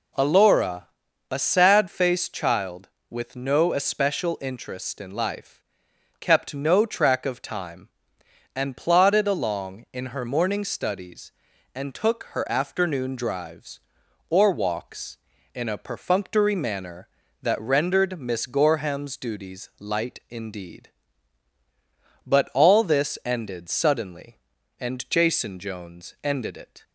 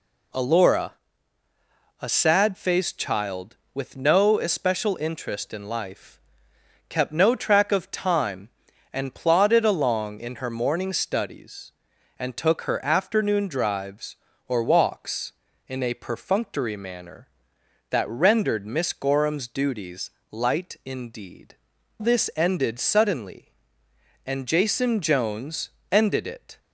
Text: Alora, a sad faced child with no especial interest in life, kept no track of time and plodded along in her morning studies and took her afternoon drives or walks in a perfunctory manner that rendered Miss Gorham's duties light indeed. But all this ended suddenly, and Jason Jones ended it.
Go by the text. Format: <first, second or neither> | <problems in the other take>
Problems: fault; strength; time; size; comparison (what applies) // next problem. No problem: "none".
first | pauses between "duties" and "light"; slight; at 20.1 s; 0.20 s long // skips "But all"; at 21.7 s // pauses between "Jones" and "ended"; slight; at 25.7 s; 0.20 s long